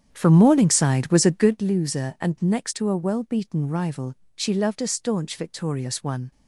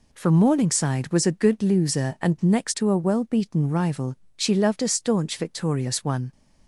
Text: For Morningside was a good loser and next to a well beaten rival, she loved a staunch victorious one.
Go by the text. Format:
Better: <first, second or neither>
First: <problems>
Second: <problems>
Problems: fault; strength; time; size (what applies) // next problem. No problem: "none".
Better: second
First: starts louder than the rest; strong; until 1.6 s; 8.5 dB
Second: none